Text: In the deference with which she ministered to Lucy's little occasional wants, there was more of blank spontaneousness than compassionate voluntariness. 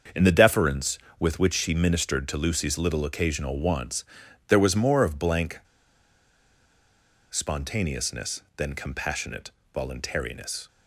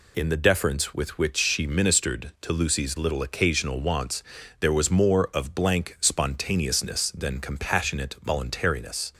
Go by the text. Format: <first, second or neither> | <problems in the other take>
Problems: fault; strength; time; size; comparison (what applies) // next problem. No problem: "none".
second | starts louder than the rest; until 1.3 s; 7 dB // pauses between "blank" and "spontaneousness"; strong; at 5.5 s; 1.7 s long // pauses between "compassionate" and "voluntariness"; slight; at 9.5 s; 0.22 s long